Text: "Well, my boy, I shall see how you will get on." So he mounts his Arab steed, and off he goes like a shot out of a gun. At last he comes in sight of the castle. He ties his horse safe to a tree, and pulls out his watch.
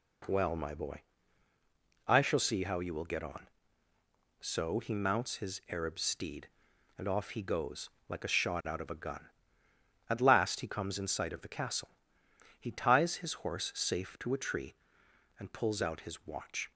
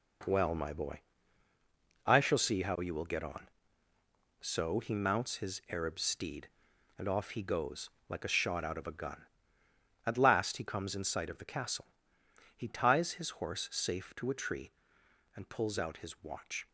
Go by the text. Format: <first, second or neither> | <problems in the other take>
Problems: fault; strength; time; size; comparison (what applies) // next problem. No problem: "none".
first | gets quieter; strong; throughout; 9 dB // pauses between "goes" and "like"; slight; at 7.8 s; 0.18 s long; slight in the first